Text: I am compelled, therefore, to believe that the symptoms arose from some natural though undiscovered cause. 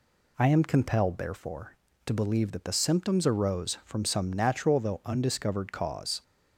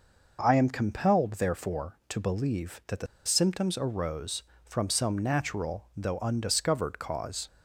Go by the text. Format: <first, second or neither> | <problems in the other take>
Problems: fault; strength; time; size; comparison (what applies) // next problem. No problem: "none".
first | pauses between "the" and "symptoms"; slight; at 3.0 s; 0.20 s long